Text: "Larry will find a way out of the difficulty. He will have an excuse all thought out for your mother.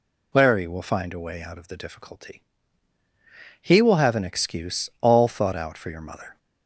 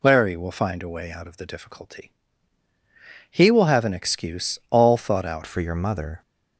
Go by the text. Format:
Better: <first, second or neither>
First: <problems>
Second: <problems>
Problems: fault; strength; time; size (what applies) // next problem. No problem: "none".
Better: first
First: none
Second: changes voice at "for"; from 5.4 s on; 0.8 s long